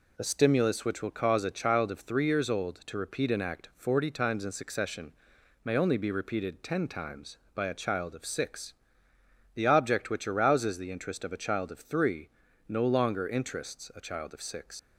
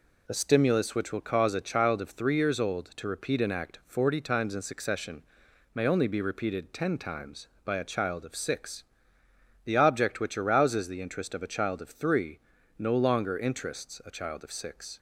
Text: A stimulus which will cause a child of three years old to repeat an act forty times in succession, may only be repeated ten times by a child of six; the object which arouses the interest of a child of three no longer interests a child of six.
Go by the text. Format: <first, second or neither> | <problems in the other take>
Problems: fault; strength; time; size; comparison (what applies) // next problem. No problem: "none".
second | pauses between "three" and "no"; slight; at 12.2 s; 0.36 s long; slight in the second // leaves "six" unfinished; at 14.7 s; 85 ms